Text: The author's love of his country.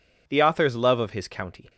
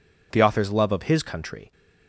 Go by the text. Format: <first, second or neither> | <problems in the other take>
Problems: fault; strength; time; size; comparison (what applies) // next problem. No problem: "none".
second | says "county" for "country"; at 1.2 s